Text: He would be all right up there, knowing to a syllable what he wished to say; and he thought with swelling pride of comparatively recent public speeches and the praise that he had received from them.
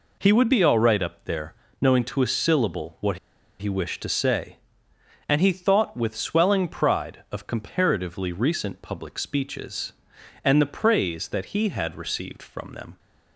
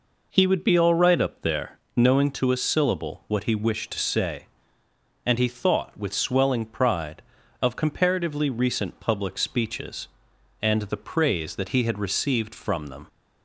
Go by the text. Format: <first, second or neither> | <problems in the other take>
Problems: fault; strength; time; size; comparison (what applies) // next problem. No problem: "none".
second | pauses between "what" and "he"; at 3.1 s; 0.42 s long